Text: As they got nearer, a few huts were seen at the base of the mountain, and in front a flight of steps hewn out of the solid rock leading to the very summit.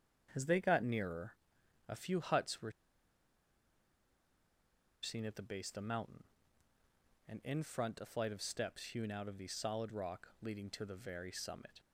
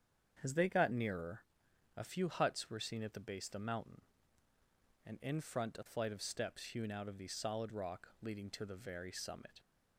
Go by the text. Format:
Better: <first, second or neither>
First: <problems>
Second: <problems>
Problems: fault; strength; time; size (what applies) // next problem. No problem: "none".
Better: second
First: starts louder than the rest; strong; until 1.9 s; 7.5 dB // pauses between "were" and "seen"; strong; at 2.6 s; 2.3 s long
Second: starts louder than the rest; strong; until 1.9 s; 7.5 dB